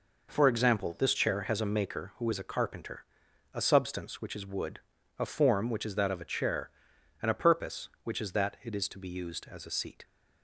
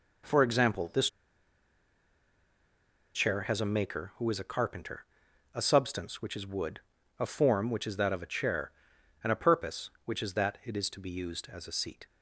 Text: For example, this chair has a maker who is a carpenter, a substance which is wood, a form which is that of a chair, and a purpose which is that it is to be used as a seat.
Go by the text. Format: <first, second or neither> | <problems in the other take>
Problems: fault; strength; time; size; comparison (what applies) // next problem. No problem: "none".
first | pauses between "this" and "chair"; strong; at 1.0 s; 2.0 s long